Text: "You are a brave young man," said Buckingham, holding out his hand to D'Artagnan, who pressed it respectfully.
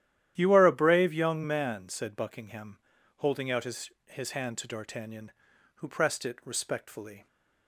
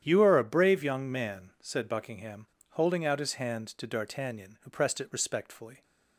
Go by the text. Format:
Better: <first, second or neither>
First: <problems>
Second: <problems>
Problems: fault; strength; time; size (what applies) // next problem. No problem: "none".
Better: second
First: starts louder than the rest; strong; until 1.3 s; 12 dB // says "his" twice; at 4.0 s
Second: starts louder than the rest; strong; until 1.0 s; 9.5 dB